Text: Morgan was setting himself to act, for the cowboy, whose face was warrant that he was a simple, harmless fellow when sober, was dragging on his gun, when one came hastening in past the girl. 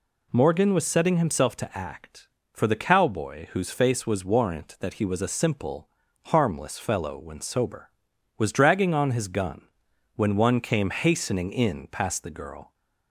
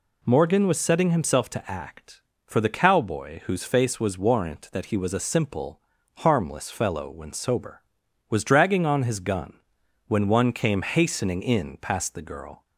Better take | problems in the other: neither | none

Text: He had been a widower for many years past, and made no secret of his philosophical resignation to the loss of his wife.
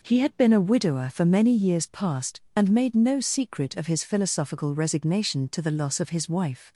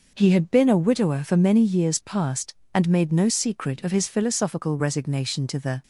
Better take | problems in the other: first | stops before "loss of his wife"; at 5.8 s

